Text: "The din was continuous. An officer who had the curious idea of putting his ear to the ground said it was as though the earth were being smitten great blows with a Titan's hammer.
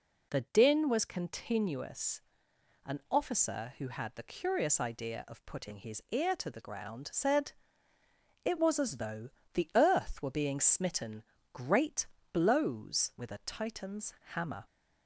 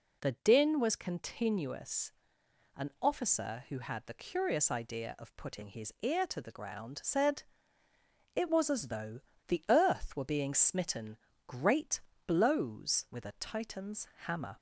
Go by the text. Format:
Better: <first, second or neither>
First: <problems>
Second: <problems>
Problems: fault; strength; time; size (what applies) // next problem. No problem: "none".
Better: neither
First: pauses between "said" and "it"; noticeable; at 7.5 s; 0.90 s long // pauses between "though" and "the"; slight; at 9.2 s; 0.24 s long // pauses between "smitten" and "great"; slight; at 11.2 s; 0.30 s long // pauses between "great" and "blows"; slight; at 12.0 s; 0.26 s long // pauses between "Titan's" and "hammer"; slight; at 14.1 s; 0.20 s long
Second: pauses between "said" and "it"; noticeable; at 7.4 s; 0.90 s long // pauses between "though" and "the"; slight; at 9.1 s; 0.27 s long // pauses between "smitten" and "great"; slight; at 11.1 s; 0.30 s long // pauses between "great" and "blows"; slight; at 12.0 s; 0.26 s long // pauses between "Titan's" and "hammer"; slight; at 14.0 s; 0.18 s long